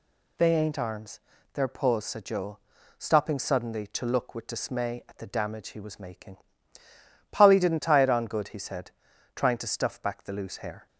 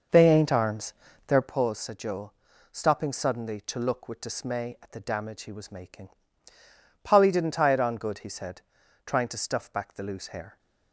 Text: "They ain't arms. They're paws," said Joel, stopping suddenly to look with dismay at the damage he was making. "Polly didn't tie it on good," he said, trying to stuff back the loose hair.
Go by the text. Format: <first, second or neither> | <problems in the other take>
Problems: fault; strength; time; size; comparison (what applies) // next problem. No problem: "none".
first | starts louder than the rest; noticeable; until 1.5 s; 6 dB